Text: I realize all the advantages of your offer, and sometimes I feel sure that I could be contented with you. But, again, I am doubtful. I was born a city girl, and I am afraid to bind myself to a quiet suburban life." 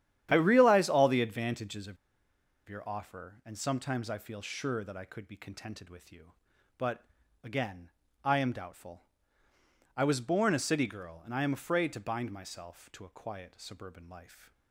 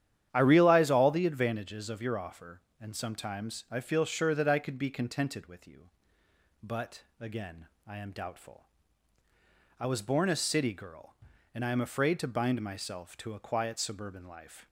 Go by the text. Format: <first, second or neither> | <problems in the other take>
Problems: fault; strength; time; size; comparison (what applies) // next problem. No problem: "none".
second | starts louder than the rest; strong; until 1.3 s; 10.5 dB; strong in the second // pauses between "of" and "your"; noticeable; at 1.9 s; 0.72 s long